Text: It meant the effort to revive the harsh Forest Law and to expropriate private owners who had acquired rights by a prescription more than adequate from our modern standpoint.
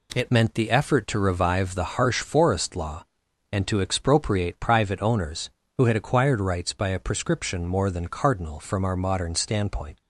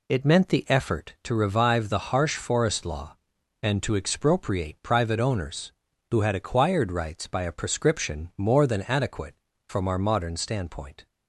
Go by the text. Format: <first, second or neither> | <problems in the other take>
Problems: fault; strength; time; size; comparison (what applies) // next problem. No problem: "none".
second | says "cardinal" for "adequate"; at 8.0 s